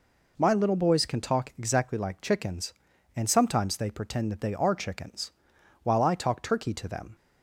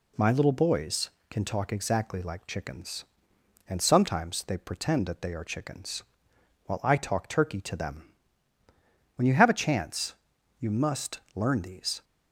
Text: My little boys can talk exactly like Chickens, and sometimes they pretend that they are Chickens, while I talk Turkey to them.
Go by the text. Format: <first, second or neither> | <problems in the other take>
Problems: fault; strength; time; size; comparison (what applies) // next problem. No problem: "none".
first | goes on to say "When you have a chance you must learn these"; strong; from 9.1 s on; 2.8 s long